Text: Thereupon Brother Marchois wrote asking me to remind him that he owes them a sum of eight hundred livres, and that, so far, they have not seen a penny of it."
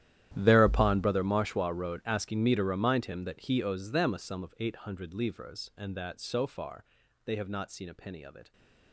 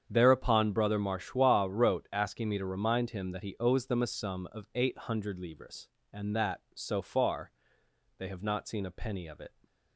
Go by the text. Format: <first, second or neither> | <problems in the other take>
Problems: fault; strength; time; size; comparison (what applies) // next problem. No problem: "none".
second | gets quieter; strong; throughout; 19 dB // starts louder than the rest; strong; until 1.3 s; 11.5 dB; strong in the second